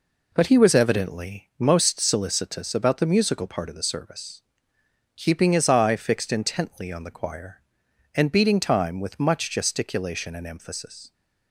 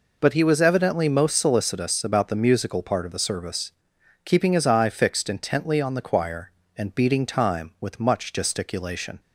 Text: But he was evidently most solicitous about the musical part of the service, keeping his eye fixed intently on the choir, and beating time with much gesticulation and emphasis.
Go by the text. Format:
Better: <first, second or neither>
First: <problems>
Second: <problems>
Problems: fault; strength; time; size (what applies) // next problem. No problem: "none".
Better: first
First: none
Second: stops before "and emphasis"; at 9.2 s